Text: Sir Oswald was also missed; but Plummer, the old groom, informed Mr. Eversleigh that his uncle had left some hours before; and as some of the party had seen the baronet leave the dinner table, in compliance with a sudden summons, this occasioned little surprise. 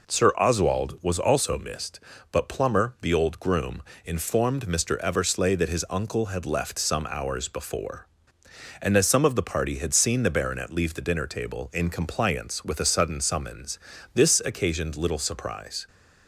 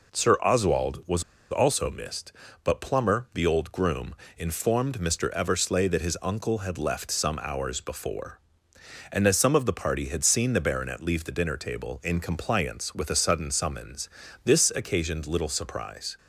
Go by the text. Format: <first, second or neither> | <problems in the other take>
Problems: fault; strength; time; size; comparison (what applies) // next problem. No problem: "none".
first | pauses between "was" and "also"; slight; at 1.2 s; 0.28 s long